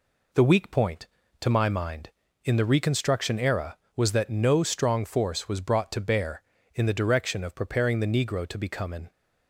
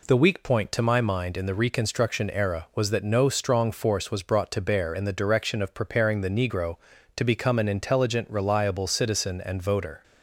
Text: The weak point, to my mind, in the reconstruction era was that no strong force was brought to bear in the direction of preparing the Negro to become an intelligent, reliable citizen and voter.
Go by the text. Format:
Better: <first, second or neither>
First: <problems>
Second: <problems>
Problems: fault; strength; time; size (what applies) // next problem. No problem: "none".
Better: second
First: stops before "intelligent reliable citizen and voter"; at 9.1 s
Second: none